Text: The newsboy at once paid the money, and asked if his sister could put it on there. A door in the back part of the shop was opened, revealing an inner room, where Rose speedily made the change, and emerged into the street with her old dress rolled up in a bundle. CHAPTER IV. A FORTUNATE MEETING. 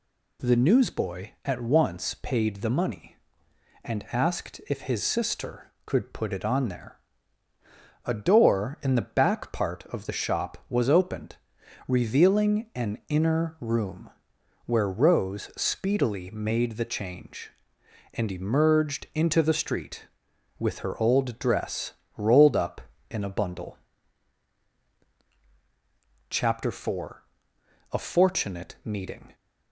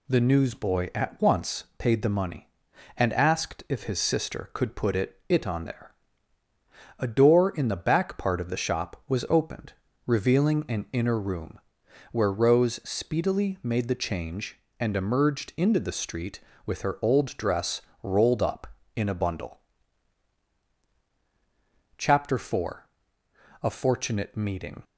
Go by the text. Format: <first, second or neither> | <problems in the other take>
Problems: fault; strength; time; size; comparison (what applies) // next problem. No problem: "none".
first | says "it" twice; at 5.2 s // pauses between "dress" and "rolled"; slight; at 17.7 s; 0.22 s long; slight in the first